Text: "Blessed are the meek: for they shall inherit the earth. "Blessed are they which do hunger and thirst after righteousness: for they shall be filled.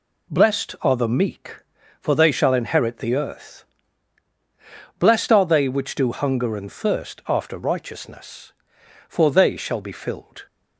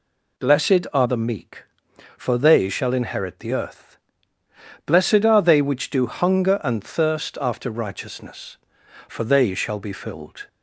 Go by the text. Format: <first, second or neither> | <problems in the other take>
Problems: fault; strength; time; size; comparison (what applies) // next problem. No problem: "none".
neither | none